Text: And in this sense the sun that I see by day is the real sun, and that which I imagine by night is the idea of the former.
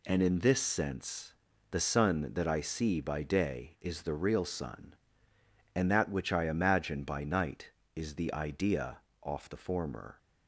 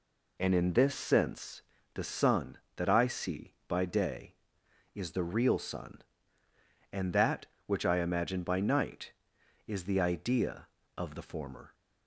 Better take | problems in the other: second | pauses between "sense" and "the"; slight; at 1.3 s; 0.36 s long; slight in the second // says "off" for "of"; at 9.2 s

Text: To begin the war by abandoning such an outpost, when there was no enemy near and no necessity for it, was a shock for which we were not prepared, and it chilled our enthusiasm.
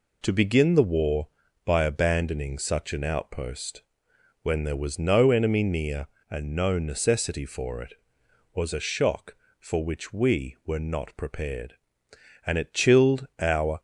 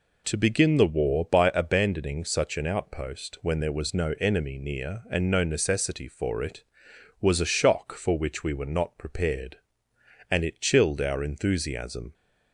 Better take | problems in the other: second | stops before "enthusiasm"; at 13.7 s

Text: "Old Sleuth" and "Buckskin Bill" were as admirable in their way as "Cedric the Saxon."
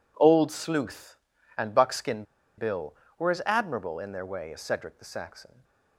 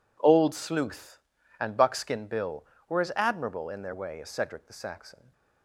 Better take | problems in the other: second | pauses between "Buckskin" and "Bill"; slight; at 2.2 s; 0.34 s long // stays silent after the last word; slight; from 5.4 s on; 0.5 s long

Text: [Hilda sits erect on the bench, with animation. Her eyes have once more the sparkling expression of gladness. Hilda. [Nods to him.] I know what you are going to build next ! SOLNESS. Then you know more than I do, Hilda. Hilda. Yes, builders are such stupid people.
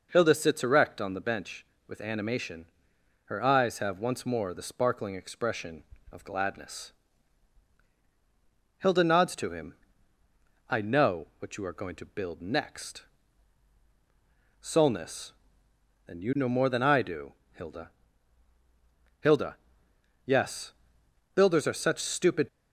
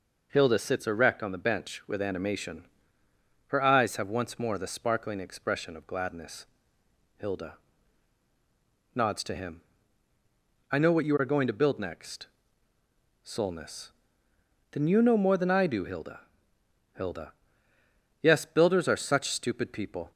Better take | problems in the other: second | stops before "people"; at 22.4 s

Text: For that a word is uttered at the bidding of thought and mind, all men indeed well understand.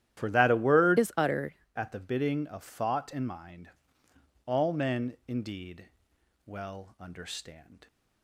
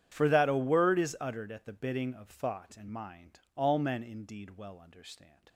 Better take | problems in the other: second | starts louder than the rest; strong; until 1.2 s; 11.5 dB; strong in the second // changes voice from "is" to "uttered"; from 0.9 to 1.5 s; 0.6 s long // pauses between "indeed" and "well"; noticeable; at 5.8 s; 0.60 s long

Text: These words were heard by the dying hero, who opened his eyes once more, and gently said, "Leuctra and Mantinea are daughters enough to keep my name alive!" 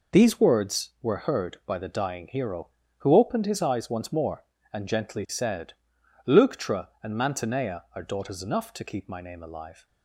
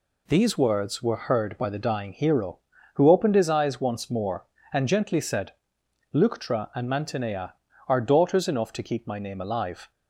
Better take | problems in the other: neither | none

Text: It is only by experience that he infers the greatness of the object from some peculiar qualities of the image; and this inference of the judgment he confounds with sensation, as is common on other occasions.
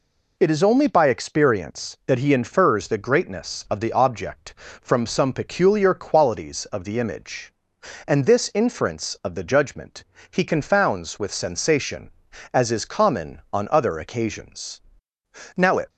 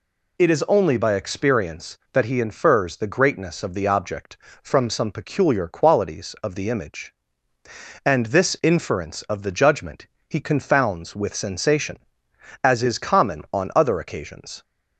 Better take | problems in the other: second | pauses between "judgment" and "he"; slight; at 10.0 s; 0.28 s long; slight in the second // goes on to say "Now it"; slight; from 15.5 s on; 0.32 s long

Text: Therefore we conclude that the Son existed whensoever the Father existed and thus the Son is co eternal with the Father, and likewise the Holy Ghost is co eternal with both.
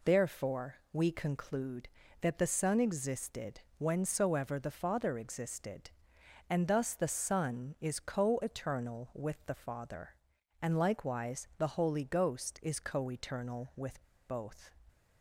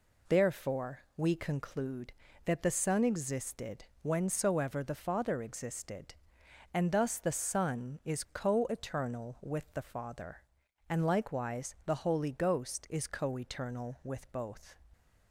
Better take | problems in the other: second | pauses between "Therefore" and "we"; slight; at 0.7 s; 0.16 s long; slight in the second // pauses between "existed" and "whensoever"; slight; at 3.6 s; 0.18 s long; slight in the second // pauses between "with" and "both"; slight; at 14.0 s; 0.24 s long

